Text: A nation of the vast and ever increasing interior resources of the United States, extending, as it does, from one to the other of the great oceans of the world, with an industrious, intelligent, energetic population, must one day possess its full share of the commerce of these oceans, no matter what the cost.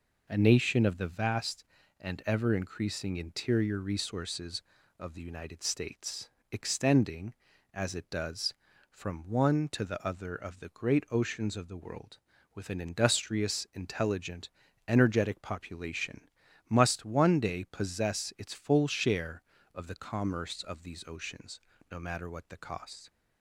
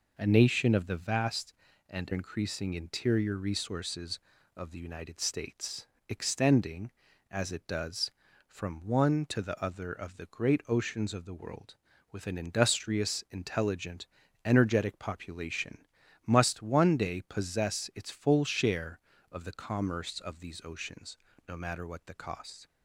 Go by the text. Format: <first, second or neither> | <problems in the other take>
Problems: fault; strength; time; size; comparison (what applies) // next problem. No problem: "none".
first | skips "ever"; at 2.1 s